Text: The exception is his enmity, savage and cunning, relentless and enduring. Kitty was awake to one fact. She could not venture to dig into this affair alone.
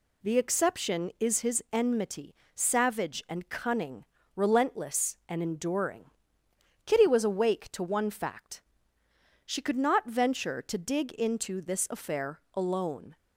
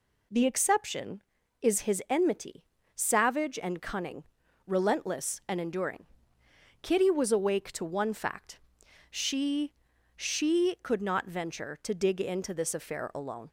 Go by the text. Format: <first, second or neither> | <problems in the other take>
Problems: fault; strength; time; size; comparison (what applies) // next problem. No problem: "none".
first | says "She" twice; at 10.1 s